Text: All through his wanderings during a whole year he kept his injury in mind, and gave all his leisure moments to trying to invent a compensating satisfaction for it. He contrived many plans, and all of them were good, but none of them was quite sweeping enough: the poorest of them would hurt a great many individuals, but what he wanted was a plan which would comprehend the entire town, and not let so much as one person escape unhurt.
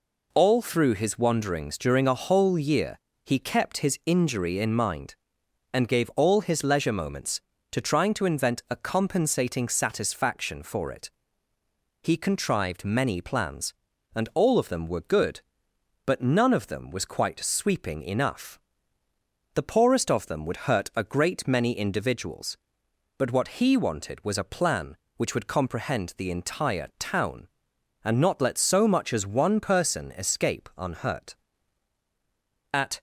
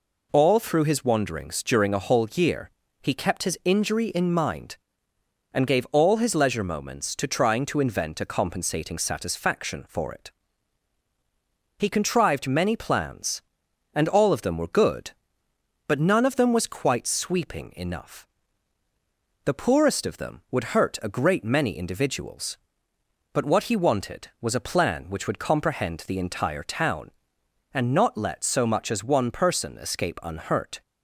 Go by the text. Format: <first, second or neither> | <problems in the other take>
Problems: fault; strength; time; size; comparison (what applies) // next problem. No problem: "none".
second | pauses between "year" and "he"; slight; at 2.9 s; 0.26 s long; slight in the second // goes on to say "At"; slight; from 32.7 s on; 0.28 s long